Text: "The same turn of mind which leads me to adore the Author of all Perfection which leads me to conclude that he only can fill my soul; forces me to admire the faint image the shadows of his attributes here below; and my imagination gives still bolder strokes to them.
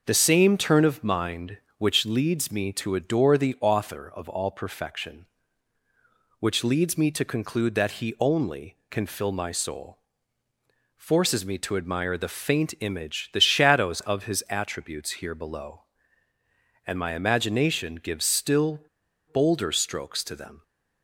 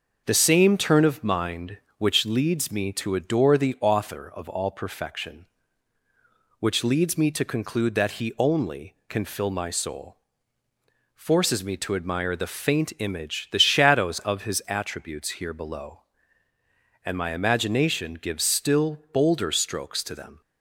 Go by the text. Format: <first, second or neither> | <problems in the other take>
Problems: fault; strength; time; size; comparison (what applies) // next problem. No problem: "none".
second | pauses between "still" and "bolder"; noticeable; at 18.8 s; 0.50 s long